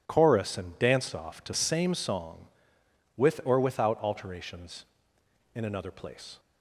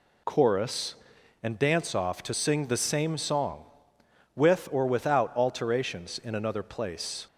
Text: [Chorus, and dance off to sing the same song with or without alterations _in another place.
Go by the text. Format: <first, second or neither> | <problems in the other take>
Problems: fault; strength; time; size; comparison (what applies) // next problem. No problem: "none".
second | skips "sing the"; at 1.5 s